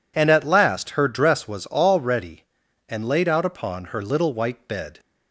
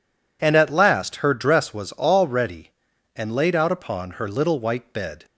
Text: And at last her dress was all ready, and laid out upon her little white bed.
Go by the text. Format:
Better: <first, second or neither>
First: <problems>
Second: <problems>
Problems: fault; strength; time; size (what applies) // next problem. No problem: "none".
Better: neither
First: none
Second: none